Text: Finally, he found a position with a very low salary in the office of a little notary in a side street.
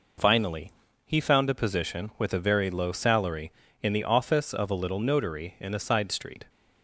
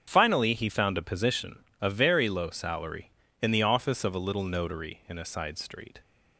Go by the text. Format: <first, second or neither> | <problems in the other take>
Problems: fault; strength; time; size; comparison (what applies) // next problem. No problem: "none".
first | starts louder than the rest; strong; until 1.0 s; 8 dB // skips "with"; at 1.7 s